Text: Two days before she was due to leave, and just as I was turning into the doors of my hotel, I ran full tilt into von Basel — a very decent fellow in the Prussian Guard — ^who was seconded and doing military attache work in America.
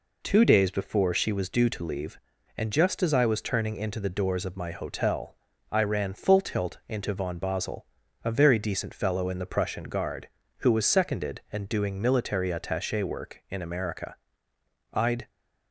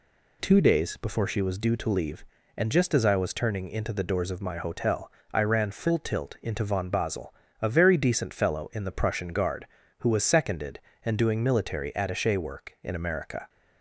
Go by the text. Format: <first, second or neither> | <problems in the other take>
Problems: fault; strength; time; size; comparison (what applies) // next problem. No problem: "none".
second | goes on to say "I'd"; slight; from 14.9 s on; 0.36 s long